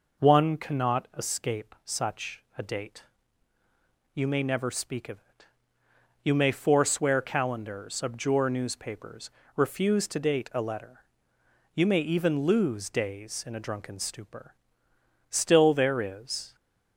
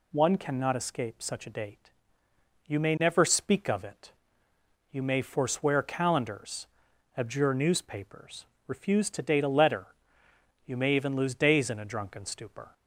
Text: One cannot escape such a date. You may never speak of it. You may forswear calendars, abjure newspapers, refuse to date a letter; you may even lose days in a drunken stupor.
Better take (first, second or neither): second